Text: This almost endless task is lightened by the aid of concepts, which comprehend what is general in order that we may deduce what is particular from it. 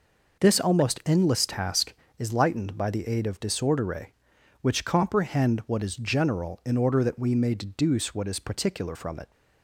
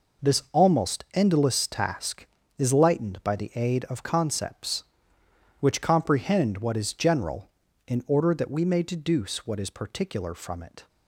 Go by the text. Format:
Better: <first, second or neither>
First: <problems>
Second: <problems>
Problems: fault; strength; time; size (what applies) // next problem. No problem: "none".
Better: second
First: says "disordere" for "concepts"; at 3.3 s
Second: none